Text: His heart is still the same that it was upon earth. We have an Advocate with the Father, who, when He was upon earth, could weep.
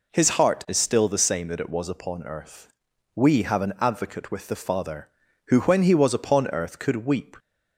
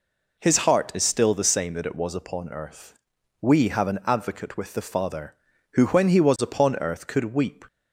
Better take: neither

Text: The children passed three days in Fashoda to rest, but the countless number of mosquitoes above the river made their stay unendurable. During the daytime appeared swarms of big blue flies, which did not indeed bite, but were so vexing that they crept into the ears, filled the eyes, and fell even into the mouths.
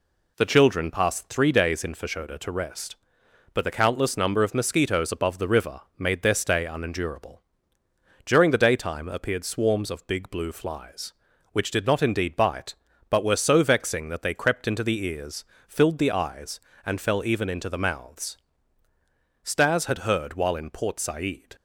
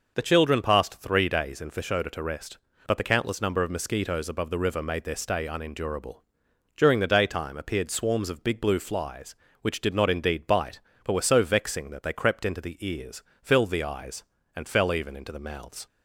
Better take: second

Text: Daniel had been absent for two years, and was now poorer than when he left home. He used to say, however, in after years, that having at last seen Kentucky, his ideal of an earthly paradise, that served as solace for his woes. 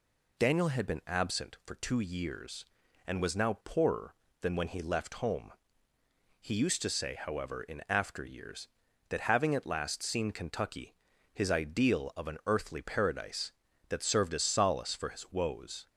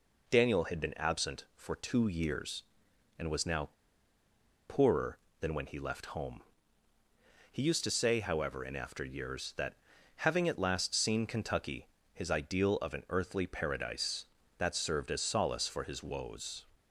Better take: first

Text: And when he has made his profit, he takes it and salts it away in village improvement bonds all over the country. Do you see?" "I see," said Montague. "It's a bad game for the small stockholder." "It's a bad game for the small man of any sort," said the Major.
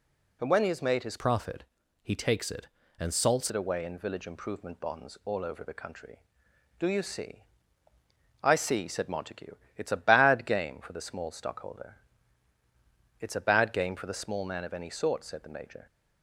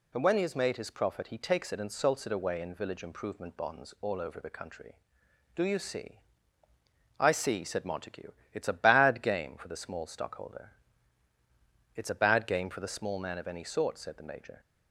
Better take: second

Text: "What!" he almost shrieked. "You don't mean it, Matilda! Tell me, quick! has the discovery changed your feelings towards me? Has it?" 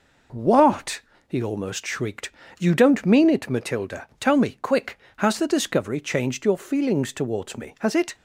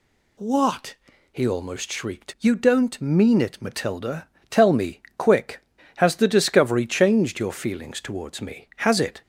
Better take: neither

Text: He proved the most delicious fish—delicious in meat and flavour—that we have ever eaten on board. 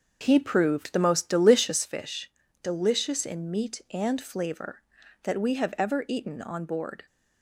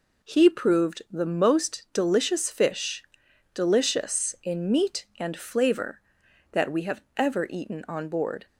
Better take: second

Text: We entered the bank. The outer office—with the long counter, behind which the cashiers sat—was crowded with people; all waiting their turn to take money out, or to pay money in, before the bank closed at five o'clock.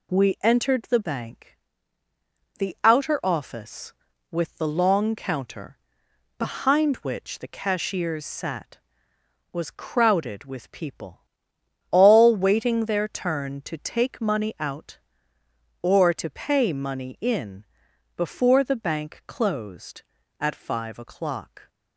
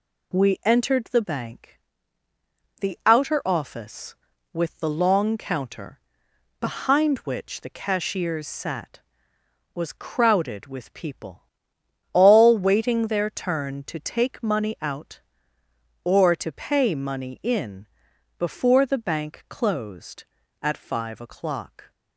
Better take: neither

